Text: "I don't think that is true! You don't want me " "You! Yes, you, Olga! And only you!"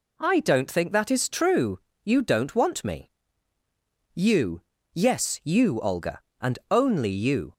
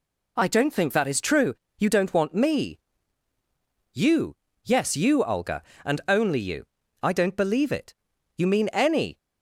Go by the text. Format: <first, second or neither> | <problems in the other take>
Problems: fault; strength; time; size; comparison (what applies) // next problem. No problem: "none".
first | goes on to say "I don't believe it You mean any"; strong; from 7.0 s on; 2.1 s long